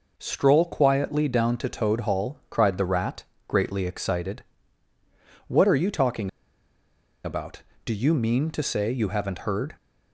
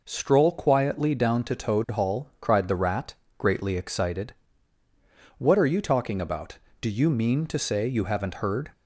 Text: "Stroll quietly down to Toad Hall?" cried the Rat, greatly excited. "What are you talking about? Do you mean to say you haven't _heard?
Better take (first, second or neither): second